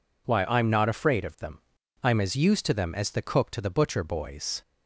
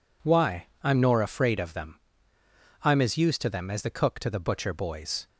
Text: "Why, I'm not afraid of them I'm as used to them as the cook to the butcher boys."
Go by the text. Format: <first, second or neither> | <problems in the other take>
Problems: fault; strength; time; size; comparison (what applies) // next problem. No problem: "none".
first | says "nor" for "not"; at 1.0 s // pauses between "them" and "I'm"; noticeable; at 1.9 s; 0.84 s long; also in the first